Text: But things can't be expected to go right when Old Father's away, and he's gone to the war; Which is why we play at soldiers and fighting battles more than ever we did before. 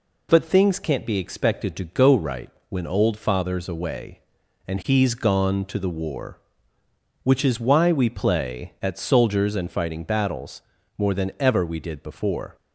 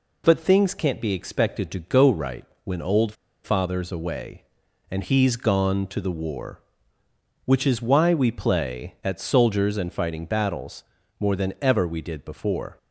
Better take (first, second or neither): first